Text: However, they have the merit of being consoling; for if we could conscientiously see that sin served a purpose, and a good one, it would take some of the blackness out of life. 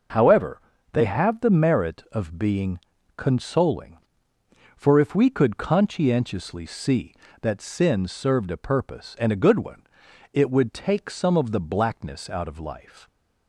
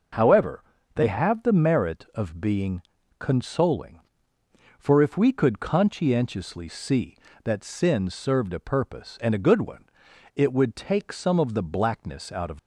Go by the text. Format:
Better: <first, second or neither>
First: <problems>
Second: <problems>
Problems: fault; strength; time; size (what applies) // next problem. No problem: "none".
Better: first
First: pauses between "being" and "consoling"; slight; at 2.7 s; 0.36 s long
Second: pauses between "being" and "consoling"; slight; at 2.8 s; 0.36 s long // stops before "life"; at 12.5 s